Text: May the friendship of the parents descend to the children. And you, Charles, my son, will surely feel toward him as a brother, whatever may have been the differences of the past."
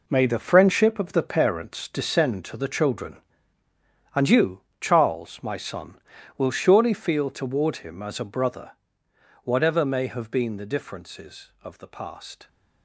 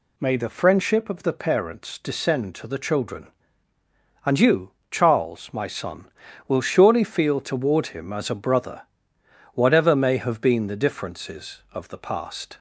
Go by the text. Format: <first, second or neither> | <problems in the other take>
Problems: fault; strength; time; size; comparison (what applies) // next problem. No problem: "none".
second | gets quieter; strong; throughout; 10.5 dB